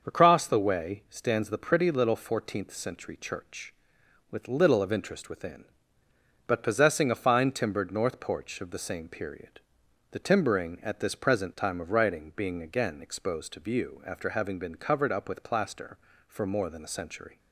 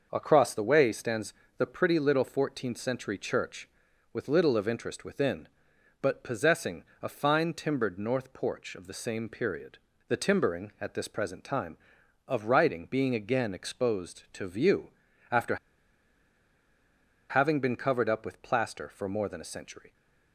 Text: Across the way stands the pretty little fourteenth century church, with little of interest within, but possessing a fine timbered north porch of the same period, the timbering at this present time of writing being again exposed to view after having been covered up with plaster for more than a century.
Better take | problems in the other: first | starts louder than the rest; noticeable; until 1.1 s; 6 dB; also in the first // pauses between "stands" and "the"; slight; at 1.3 s; 0.24 s long // pauses between "possessing" and "a"; slight; at 6.8 s; 0.16 s long // pauses between "view" and "after"; at 14.8 s; 0.40 s long // pauses between "after" and "having"; strong; at 15.5 s; 1.7 s long

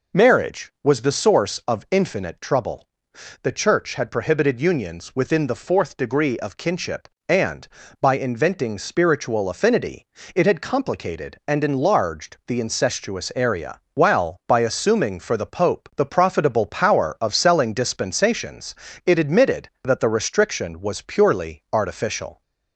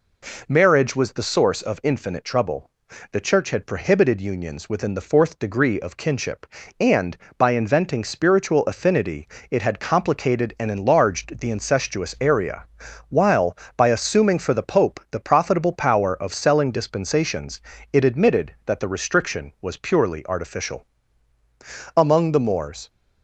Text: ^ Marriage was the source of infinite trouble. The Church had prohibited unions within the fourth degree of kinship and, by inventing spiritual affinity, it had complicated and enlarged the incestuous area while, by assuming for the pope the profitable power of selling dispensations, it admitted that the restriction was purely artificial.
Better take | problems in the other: first | pauses between "area" and "while"; noticeable; at 12.6 s; 0.46 s long // goes on to say "Among the Moors"; noticeable; from 21.9 s on; 0.92 s long

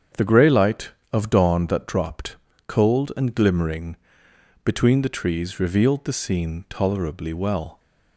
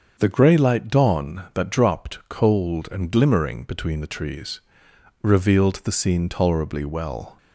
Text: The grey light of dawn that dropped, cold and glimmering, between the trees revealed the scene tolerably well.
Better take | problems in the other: first | starts louder than the rest; until 1.2 s; 6.5 dB; strong in the first // skips "of"; at 0.8 s // pauses between "trees" and "revealed"; noticeable; at 4.6 s; 0.60 s long

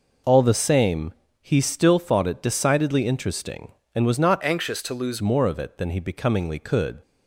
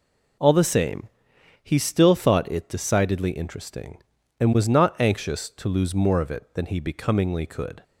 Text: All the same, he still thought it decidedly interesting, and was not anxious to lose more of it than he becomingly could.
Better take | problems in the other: second | changes voice from "anxious" to "lose"; from 4.4 to 5.2 s; 0.8 s long

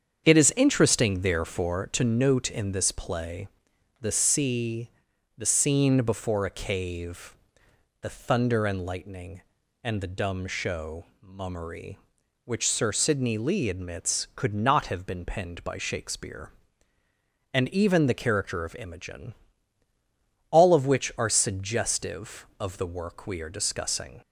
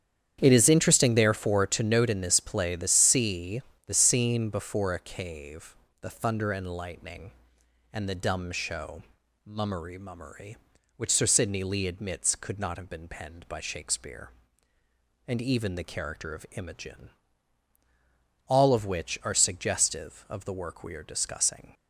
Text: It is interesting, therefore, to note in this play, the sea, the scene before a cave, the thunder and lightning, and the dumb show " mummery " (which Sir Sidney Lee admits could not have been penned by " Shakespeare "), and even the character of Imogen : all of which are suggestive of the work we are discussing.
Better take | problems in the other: first | starts louder than the rest; strong; until 1.4 s; 9 dB; strong in the first // says "mummery" twice; at 9.9 s

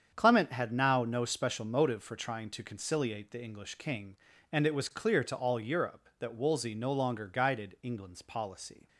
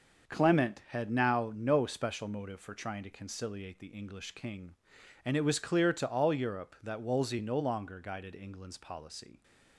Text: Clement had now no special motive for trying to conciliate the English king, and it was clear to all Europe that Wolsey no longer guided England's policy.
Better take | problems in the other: neither | starts louder than the rest; the same in both

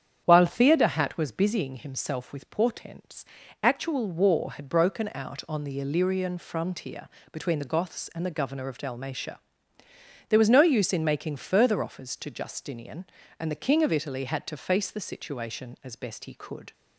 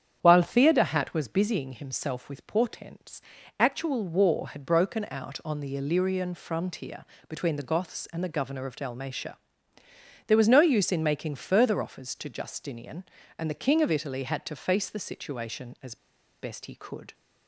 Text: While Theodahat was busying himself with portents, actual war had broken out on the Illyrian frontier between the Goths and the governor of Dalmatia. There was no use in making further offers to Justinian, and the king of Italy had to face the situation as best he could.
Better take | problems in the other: first | starts louder than the rest; strong; until 1.2 s; 8 dB; strong in the first // pauses between "frontier" and "between"; slight; at 7.0 s; 0.22 s long; slight in the first // pauses between "as" and "best"; at 15.9 s; 0.45 s long

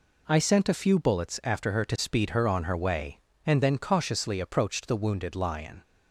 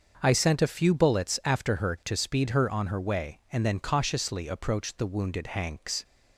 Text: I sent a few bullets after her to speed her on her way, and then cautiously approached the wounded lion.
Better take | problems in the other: first | starts louder than the rest; until 1.2 s; 6.5 dB // says "hanks" for "lion"; at 5.4 s

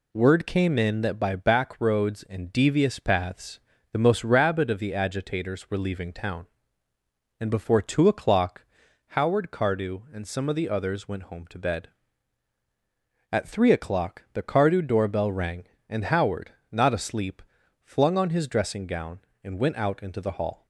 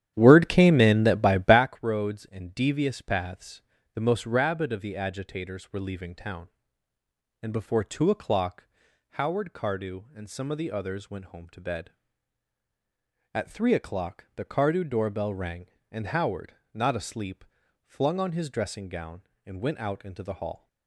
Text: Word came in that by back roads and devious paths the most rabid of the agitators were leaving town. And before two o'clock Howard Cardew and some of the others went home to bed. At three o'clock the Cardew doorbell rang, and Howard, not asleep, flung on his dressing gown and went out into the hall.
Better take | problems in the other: first | starts louder than the rest; strong; until 1.7 s; 10.5 dB // pauses between "paths" and "the"; slight; at 3.6 s; 0.32 s long; slight in the first // pauses between "o'clock" and "Howard"; noticeable; at 8.6 s; 0.48 s long; noticeable in the first

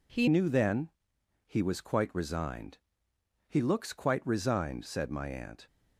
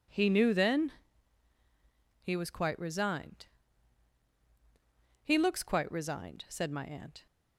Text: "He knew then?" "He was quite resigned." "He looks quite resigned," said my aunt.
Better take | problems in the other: second | changes voice at "knew"; from 0.2 s on; 5.4 s long

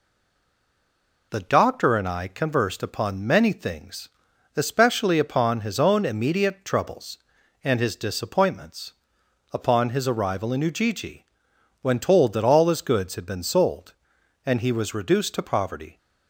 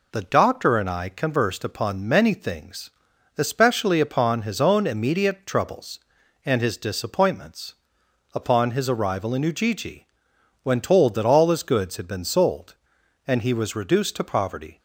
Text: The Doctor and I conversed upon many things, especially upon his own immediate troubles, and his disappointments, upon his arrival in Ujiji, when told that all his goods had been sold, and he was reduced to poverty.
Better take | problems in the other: second | stays silent before the first word; noticeable; until 1.3 s; 1.3 s long

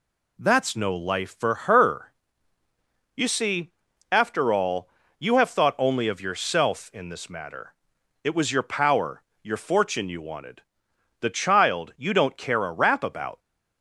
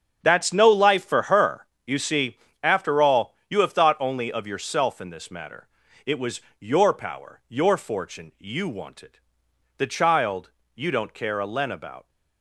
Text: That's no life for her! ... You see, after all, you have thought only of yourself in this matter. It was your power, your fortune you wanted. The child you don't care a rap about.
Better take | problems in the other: first | starts louder than the rest; strong; until 1.2 s; 7.5 dB // pauses between "was" and "your"; slight; at 6.4 s; 0.18 s long // pauses between "child" and "you"; slight; at 10.5 s; 0.24 s long // says "len" for "rap"; at 11.4 s

